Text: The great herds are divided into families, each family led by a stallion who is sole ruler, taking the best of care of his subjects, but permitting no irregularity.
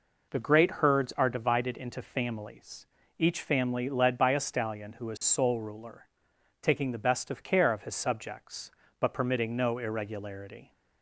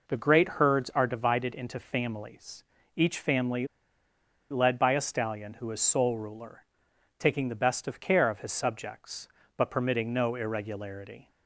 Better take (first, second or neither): first